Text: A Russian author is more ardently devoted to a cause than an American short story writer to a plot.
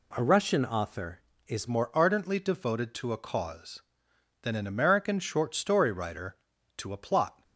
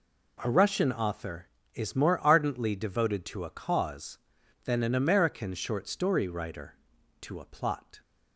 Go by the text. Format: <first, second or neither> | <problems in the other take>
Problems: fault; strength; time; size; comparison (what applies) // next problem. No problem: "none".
second | changes voice at "more"; from 1.6 s on; 5.8 s long